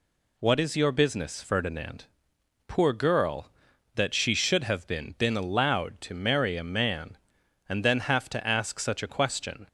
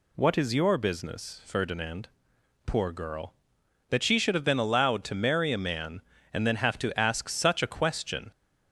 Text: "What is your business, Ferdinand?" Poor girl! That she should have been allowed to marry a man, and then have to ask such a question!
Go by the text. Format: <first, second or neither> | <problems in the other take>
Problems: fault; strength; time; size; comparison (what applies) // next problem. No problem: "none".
second | says "been" twice; at 5.1 s